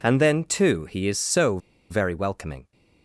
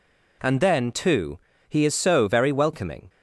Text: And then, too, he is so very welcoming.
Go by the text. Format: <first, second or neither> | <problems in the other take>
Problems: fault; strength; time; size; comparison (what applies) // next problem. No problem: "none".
second | pauses between "so" and "very"; slight; at 1.5 s; 0.32 s long